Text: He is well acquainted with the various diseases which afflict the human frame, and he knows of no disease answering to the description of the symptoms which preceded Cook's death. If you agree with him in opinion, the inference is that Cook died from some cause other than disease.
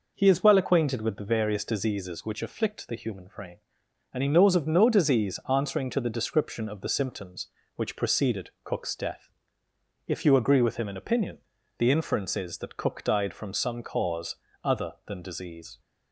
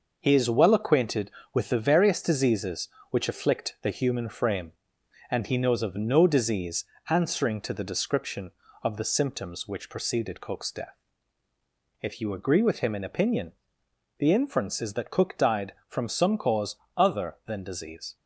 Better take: first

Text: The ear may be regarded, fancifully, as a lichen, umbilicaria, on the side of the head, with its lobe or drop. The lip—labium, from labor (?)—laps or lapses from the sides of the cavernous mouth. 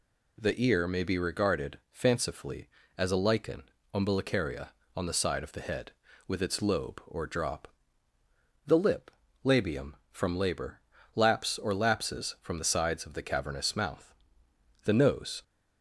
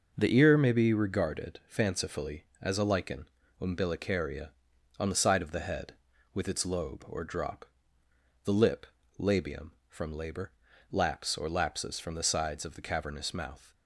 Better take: second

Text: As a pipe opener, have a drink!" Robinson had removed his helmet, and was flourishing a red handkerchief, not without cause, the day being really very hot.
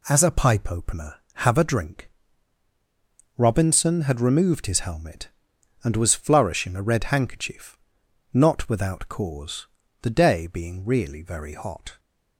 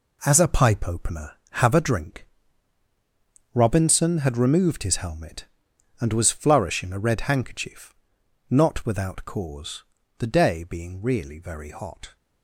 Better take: first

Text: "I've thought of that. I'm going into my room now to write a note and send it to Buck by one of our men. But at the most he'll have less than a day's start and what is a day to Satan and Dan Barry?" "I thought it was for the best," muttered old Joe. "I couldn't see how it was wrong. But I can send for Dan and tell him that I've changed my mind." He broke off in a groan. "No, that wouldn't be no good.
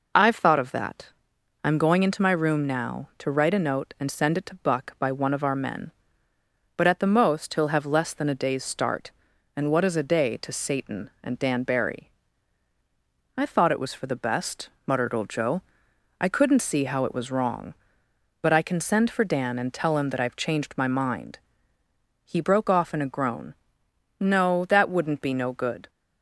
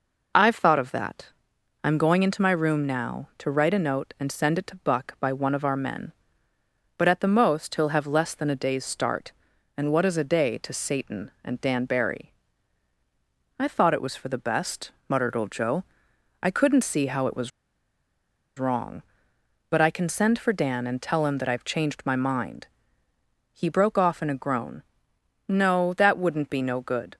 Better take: first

